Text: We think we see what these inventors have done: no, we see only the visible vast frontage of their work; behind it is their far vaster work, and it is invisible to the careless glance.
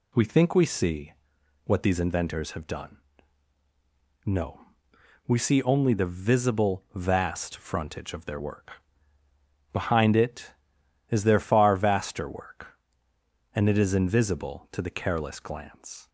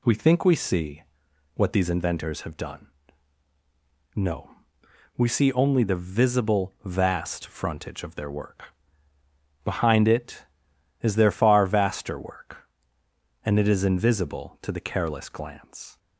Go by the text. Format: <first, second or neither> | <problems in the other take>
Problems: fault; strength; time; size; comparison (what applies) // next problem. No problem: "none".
neither | pauses between "see" and "what"; noticeable; the same in both